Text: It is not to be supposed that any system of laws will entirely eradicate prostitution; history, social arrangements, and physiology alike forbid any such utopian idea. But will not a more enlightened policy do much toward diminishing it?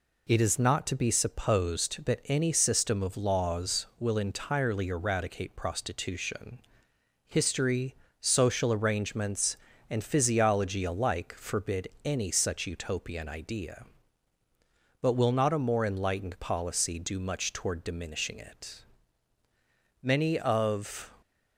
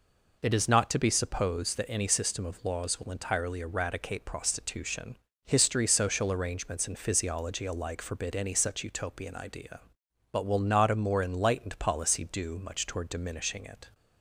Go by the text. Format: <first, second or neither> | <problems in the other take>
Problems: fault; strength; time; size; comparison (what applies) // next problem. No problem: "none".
second | pauses between "forbid" and "any"; slight; at 11.8 s; 0.16 s long // goes on to say "Many of"; noticeable; from 20.0 s on; 1.0 s long